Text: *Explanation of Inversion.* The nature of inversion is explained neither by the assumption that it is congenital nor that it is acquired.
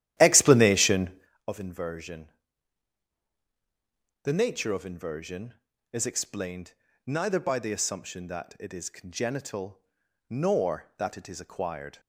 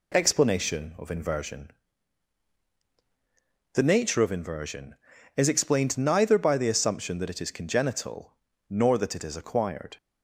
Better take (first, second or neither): second